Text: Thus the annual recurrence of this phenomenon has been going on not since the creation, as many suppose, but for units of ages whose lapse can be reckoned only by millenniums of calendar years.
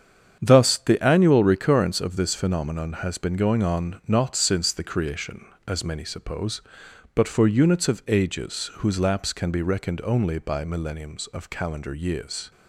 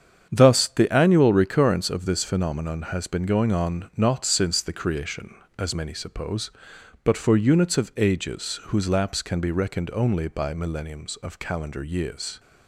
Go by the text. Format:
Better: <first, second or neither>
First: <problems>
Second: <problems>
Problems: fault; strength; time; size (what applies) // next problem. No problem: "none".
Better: neither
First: starts louder than the rest; strong; until 1.4 s; 7.5 dB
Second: starts louder than the rest; strong; until 1.3 s; 8 dB